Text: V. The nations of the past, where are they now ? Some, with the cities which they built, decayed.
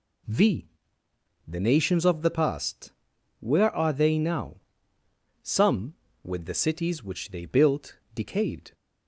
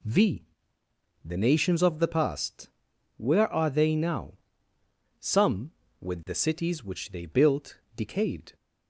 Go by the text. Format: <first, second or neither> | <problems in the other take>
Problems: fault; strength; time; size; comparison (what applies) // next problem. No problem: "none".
neither | none